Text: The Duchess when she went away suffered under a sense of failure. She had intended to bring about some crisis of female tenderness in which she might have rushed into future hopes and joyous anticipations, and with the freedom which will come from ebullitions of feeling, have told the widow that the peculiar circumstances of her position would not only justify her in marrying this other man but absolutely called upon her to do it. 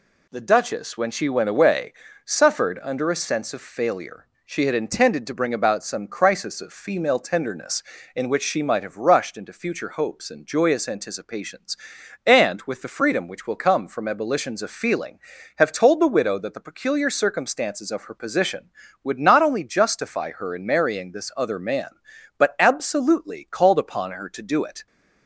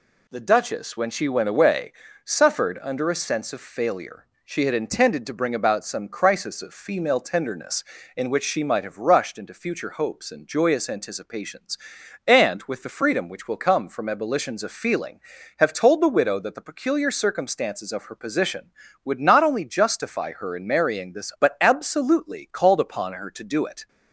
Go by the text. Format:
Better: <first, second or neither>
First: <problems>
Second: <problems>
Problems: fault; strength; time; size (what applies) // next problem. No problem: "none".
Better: first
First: pauses between "away" and "suffered"; slight; at 1.9 s; 0.32 s long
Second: pauses between "away" and "suffered"; slight; at 1.9 s; 0.32 s long // skips "other man"; at 21.3 s